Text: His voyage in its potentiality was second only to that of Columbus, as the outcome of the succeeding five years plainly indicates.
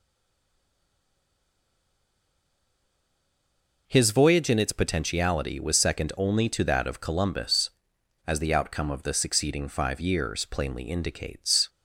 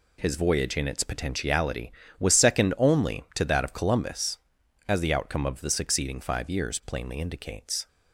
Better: second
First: stays silent before the first word; strong; until 3.8 s; 3.8 s long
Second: none

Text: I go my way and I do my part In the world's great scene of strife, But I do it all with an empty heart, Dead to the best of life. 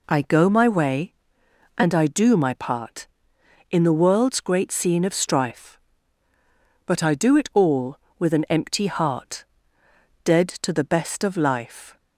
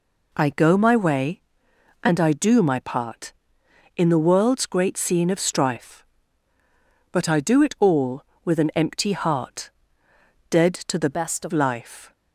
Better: first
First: none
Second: changes voice from "best" to "of"; from 11.1 to 11.5 s; 0.4 s long

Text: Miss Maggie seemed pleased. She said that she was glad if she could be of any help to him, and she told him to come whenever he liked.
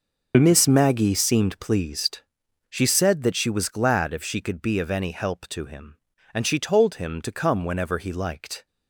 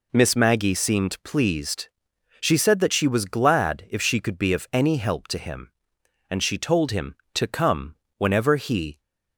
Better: first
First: none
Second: pauses between "come" and "whenever"; slight; at 7.9 s; 0.22 s long // stops before "liked"; at 8.9 s

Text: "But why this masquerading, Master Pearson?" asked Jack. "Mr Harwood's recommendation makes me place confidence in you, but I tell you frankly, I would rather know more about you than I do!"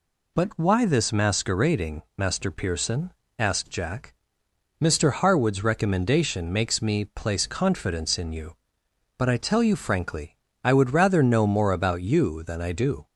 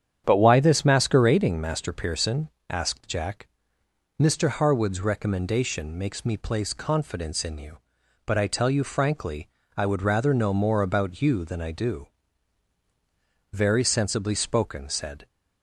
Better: first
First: none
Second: starts louder than the rest; strong; until 1.2 s; 8.5 dB // goes on to say "Very sensibly spoken said"; strong; from 13.5 s on; 1.7 s long

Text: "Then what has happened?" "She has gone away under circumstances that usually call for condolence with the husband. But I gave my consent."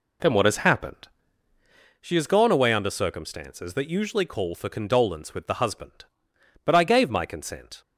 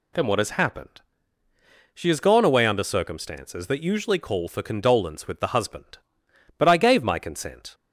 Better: second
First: starts louder than the rest; slight; until 1.9 s; 2.5 dB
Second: none

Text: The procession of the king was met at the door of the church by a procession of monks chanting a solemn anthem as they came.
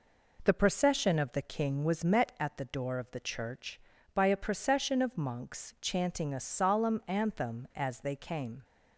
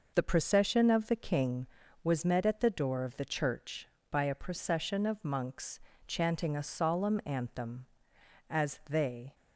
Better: first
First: none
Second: pauses between "monks" and "chanting"; slight; at 5.7 s; 0.28 s long // stops before "came"; at 9.3 s

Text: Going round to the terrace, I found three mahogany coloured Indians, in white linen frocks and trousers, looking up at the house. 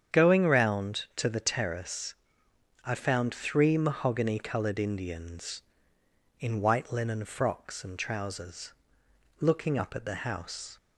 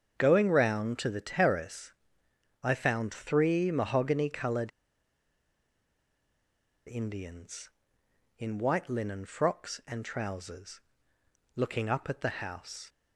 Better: first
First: starts louder than the rest; strong; until 1.2 s; 8 dB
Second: starts louder than the rest; strong; until 1.2 s; 7 dB // pauses between "coloured" and "Indians"; strong; at 4.7 s; 2.1 s long

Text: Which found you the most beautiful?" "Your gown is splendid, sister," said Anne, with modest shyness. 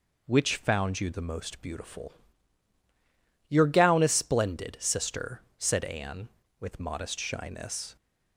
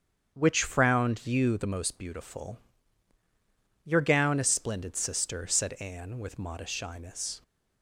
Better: first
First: none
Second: starts louder than the rest; strong; until 1.3 s; 8 dB // says "frowned" for "found"; at 0.6 s

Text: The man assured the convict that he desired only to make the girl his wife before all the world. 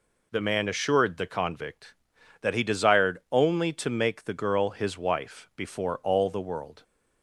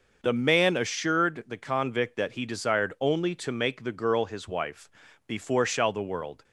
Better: first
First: none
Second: pauses between "wife" and "before"; at 4.8 s; 0.38 s long // says "shall" for "all"; at 5.6 s

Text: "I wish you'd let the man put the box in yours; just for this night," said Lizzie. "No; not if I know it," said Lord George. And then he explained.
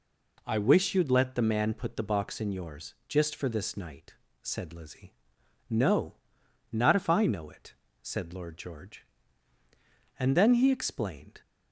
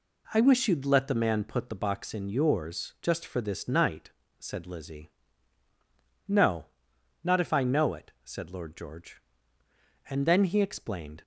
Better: neither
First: none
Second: none

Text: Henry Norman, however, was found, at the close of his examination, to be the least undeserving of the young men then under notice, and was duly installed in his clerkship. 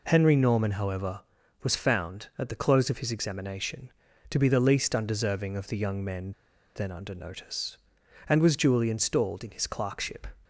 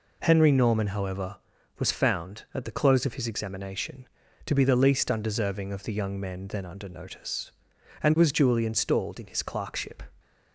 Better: second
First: pauses between "men" and "then"; at 6.3 s; 0.43 s long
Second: none

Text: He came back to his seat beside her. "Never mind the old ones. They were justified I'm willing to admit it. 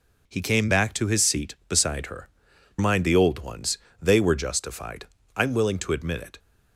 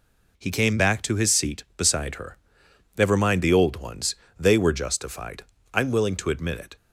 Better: second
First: skips "Never"; at 2.5 s // pauses between "justified" and "I'm"; slight; at 5.0 s; 0.28 s long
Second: pauses between "justified" and "I'm"; slight; at 5.4 s; 0.28 s long

